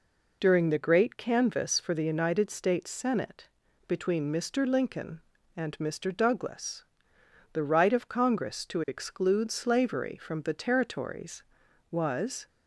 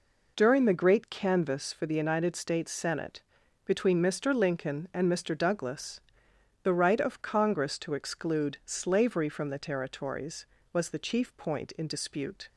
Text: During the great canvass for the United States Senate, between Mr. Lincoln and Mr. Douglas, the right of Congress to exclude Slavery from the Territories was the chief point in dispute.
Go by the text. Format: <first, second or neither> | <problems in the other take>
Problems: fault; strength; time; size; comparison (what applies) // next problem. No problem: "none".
second | stops before "the chief point in dispute"; at 12.4 s